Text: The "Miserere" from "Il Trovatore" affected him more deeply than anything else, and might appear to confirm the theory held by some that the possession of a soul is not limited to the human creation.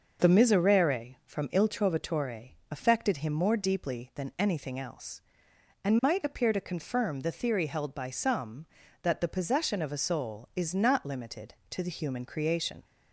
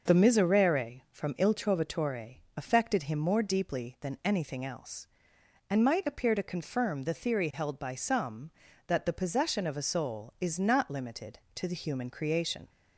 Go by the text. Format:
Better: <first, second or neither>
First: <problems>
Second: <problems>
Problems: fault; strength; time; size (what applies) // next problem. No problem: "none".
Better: neither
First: pauses between "Trovatore" and "affected"; slight; at 2.5 s; 0.18 s long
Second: pauses between "Trovatore" and "affected"; slight; at 2.3 s; 0.18 s long